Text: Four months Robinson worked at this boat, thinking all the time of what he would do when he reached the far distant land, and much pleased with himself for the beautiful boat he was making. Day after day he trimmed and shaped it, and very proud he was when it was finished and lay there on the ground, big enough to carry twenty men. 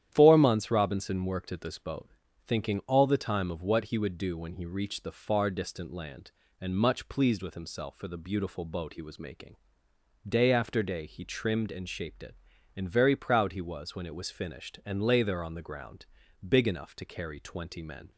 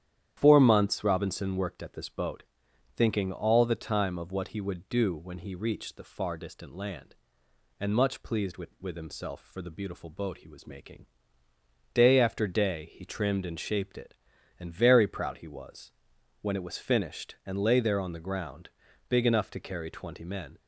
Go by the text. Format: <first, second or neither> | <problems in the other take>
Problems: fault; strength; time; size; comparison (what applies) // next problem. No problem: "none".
first | starts louder than the rest; strong; until 1.4 s; 10 dB; strong in the first // says "with" twice; at 8.8 s // pauses between "was" and "when"; noticeable; at 15.9 s; 0.50 s long